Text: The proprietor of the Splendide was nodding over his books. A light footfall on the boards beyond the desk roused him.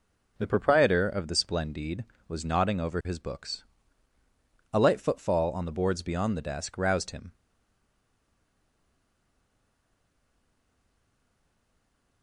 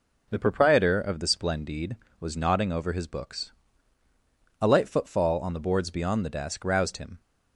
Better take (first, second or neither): second